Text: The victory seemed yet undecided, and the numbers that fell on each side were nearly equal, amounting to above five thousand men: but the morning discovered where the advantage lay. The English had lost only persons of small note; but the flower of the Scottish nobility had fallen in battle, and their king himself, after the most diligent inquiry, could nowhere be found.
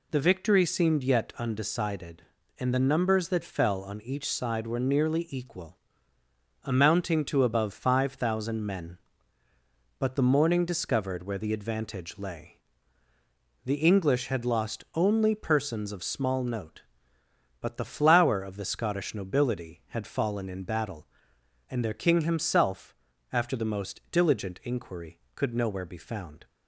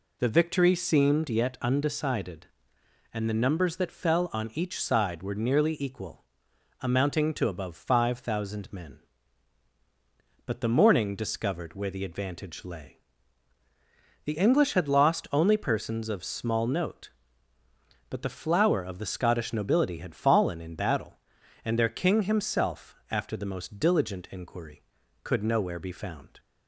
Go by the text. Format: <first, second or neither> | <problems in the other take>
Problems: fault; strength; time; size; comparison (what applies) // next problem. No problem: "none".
neither | none